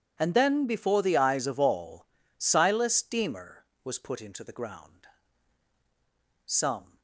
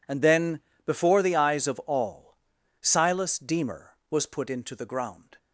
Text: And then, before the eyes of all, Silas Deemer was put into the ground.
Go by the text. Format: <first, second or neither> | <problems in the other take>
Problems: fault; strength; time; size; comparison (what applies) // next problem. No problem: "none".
second | goes on to say "Some"; from 6.4 s on; 0.54 s long